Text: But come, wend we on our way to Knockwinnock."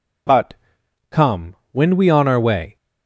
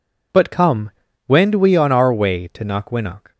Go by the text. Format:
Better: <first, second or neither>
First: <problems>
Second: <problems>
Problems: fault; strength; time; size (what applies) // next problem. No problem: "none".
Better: second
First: pauses between "But" and "come"; noticeable; at 0.5 s; 0.58 s long // stops before "to Knockwinnock"; at 2.7 s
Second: none